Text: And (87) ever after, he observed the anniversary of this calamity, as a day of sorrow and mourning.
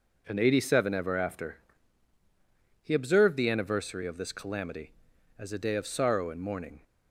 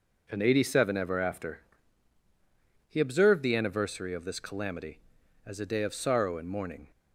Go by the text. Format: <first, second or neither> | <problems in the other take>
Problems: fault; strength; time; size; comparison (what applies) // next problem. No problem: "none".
neither | none